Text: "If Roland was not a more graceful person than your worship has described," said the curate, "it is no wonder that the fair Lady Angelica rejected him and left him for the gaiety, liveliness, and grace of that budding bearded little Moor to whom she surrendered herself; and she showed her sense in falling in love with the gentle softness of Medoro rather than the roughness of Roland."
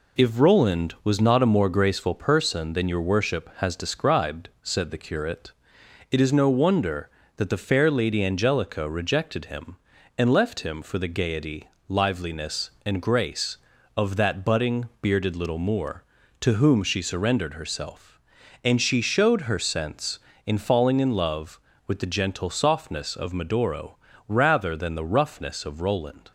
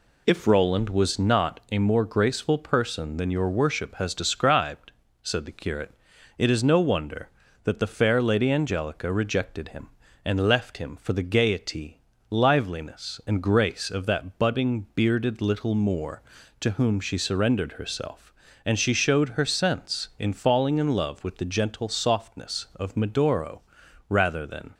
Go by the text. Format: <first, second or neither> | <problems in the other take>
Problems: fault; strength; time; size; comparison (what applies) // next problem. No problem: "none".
first | pauses between "Medoro" and "rather"; noticeable; at 23.6 s; 0.48 s long; slight in the first // stops before "the roughness of Roland"; at 24.7 s